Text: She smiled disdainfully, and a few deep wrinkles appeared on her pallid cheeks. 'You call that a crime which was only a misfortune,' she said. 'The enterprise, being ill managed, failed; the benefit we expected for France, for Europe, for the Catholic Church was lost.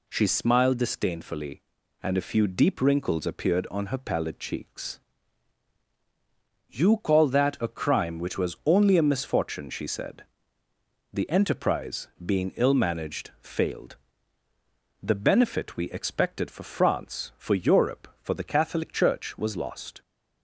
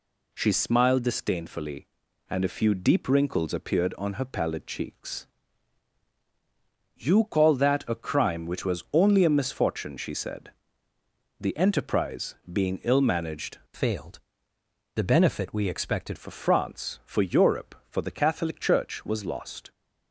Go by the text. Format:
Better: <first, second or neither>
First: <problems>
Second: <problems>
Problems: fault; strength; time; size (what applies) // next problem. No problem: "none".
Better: first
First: none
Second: changes voice from "failed" to "expected"; from 13.7 to 16.1 s; 2.4 s long